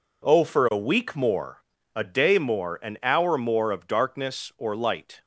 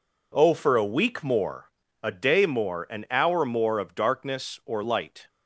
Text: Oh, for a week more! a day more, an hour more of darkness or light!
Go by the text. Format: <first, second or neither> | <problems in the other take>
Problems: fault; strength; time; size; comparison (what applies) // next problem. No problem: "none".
neither | none